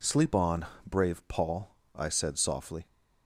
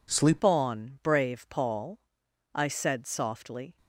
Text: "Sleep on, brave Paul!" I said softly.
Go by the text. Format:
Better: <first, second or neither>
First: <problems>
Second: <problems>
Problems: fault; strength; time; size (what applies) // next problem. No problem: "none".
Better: first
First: none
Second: changes voice at "on"; from 0.4 s on; 3.3 s long